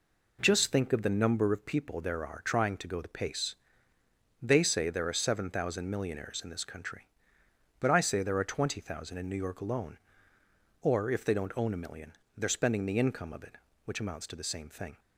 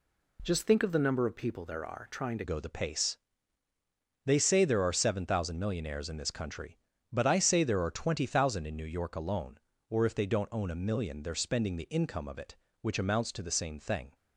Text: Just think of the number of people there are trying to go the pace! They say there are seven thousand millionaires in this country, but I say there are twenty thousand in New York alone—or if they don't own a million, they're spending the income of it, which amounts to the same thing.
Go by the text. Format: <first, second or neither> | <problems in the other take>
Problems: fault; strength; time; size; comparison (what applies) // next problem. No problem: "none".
first | changes voice at "go"; from 2.4 s on; 11.7 s long